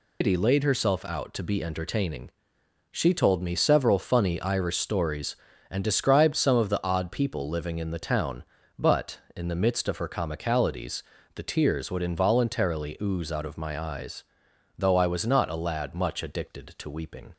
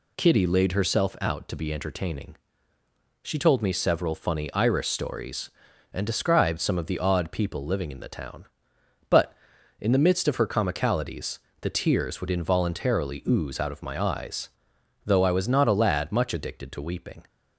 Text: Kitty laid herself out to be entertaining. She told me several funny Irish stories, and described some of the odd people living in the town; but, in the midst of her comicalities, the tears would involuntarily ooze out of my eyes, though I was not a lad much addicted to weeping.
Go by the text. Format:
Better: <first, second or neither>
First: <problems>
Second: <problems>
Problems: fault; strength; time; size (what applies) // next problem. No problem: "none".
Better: second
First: loses the start of "Kitty"; at 0.2 s; 135 ms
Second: none